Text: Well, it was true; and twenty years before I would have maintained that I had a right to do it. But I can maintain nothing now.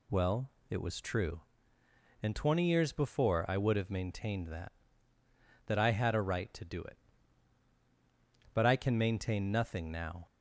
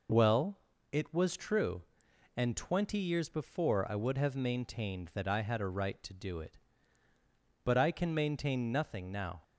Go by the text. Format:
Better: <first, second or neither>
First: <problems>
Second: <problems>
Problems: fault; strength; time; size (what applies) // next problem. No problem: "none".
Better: second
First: says "that" twice; at 5.6 s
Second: none